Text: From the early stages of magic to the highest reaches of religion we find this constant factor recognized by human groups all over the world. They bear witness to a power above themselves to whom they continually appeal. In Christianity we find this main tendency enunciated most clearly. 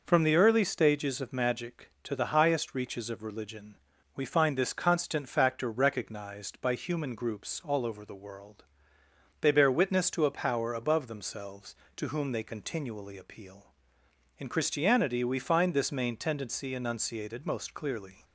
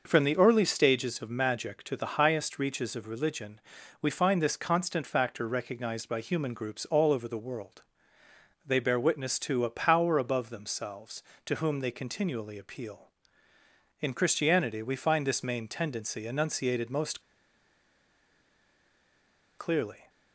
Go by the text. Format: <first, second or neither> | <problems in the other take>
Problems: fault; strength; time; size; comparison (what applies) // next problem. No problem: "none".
first | pauses between "religion" and "we"; at 3.6 s; 0.40 s long; also in the first // pauses between "most" and "clearly"; strong; at 17.2 s; 2.3 s long